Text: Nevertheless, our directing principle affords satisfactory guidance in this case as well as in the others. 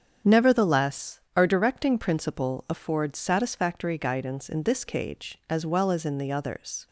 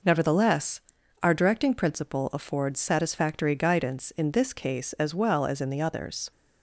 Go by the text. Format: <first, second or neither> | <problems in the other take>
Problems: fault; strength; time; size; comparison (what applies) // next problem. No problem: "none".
second | starts louder than the rest; strong; until 1.4 s; 8 dB // says "cage" for "case"; at 4.8 s